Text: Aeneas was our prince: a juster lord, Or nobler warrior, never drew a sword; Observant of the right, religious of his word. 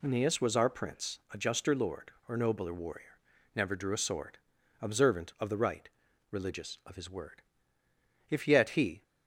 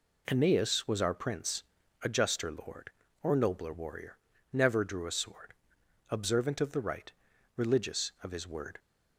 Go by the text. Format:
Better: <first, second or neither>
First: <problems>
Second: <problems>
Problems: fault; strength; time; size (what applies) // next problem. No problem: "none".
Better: second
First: goes on to say "If yet he"; noticeable; from 8.3 s on; 0.72 s long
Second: none